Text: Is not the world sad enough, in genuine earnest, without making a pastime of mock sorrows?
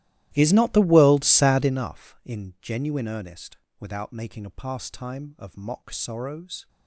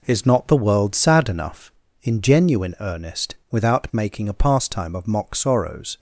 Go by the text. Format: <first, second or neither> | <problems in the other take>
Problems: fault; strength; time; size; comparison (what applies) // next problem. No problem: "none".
second | starts louder than the rest; strong; until 1.9 s; 15.5 dB